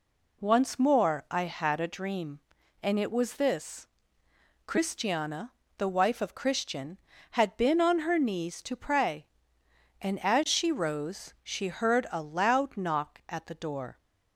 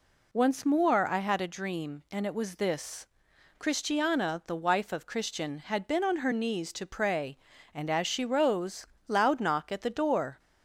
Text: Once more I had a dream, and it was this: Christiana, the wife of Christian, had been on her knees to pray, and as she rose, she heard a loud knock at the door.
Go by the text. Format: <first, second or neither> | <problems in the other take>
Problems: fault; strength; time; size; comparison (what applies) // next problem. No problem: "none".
first | skips "she heard a"; at 8.9 s